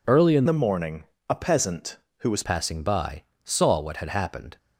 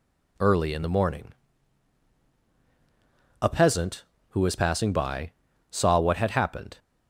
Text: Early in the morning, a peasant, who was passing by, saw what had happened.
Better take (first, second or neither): second